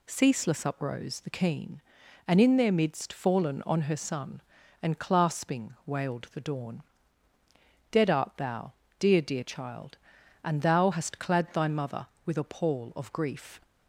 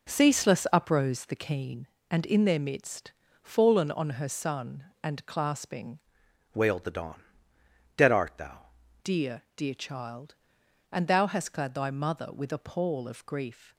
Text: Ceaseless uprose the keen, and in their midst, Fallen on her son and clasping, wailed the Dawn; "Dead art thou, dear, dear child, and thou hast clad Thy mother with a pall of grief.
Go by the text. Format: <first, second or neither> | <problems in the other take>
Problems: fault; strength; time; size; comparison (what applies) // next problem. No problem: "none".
first | changes voice from "wailed" to "thou"; from 6.5 to 8.6 s; 2.1 s long